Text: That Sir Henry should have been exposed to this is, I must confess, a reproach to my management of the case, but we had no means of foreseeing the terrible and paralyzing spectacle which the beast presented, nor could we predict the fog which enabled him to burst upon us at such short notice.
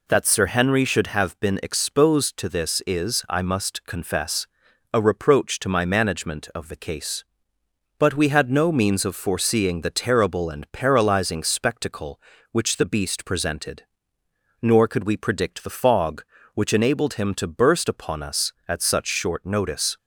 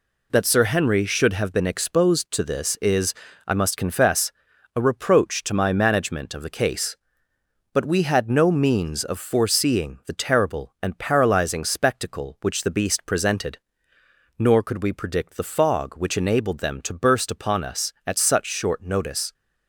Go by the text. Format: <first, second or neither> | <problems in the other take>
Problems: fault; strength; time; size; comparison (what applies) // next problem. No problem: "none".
first | says "them" for "him"; at 16.5 s